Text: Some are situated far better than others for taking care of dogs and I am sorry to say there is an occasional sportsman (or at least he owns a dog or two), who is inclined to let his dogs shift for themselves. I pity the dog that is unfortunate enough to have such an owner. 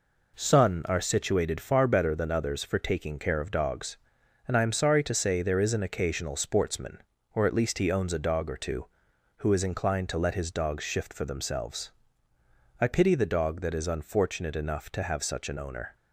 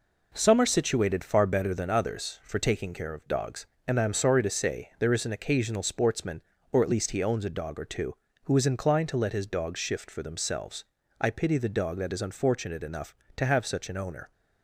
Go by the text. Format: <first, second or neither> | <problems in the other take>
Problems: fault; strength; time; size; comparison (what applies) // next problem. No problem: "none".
second | says "Sun" for "Some"; at 0.3 s